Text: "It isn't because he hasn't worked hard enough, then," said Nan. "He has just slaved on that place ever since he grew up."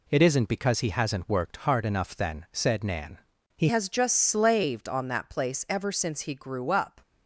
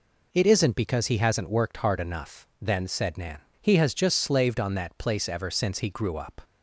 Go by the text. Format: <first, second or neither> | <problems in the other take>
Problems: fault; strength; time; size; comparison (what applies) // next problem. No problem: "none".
second | changes voice at "has"; from 3.6 s on; 3.4 s long